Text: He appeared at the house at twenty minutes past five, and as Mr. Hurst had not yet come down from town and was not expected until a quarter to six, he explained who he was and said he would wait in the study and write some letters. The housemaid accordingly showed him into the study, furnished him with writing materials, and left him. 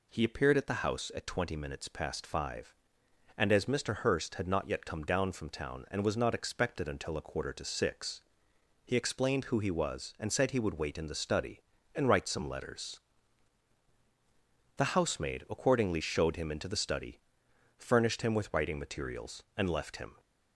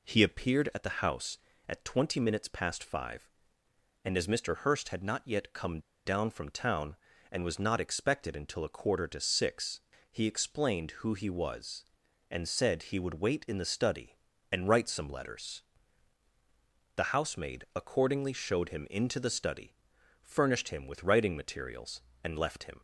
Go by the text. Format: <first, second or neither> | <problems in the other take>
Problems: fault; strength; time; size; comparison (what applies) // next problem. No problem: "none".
first | pauses between "come" and "down"; slight; at 5.7 s; 0.26 s long